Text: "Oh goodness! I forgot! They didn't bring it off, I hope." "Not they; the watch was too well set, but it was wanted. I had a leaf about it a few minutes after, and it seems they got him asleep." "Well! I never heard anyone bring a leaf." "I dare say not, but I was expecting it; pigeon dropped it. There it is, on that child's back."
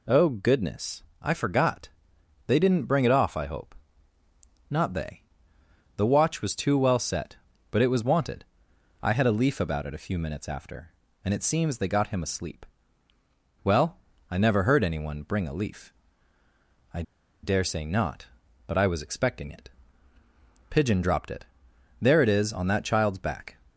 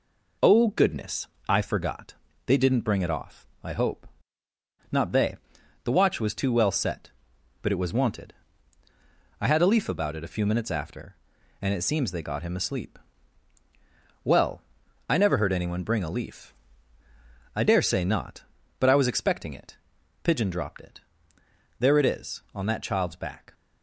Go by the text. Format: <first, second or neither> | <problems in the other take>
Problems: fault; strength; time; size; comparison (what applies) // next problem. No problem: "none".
second | pauses between "I" and "dare"; at 17.0 s; 0.40 s long